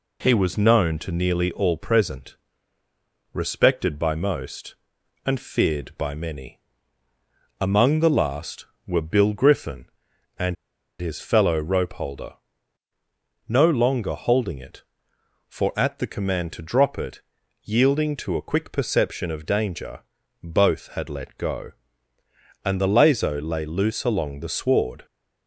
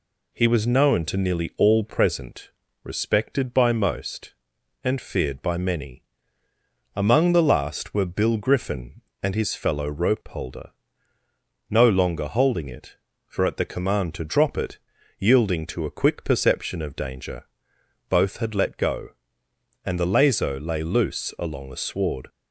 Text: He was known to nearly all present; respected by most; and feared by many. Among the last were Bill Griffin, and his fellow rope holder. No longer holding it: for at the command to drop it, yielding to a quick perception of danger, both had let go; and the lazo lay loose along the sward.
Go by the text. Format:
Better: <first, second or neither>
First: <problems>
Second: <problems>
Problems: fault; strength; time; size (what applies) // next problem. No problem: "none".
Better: second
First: pauses between "and" and "his"; noticeable; at 10.5 s; 0.46 s long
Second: none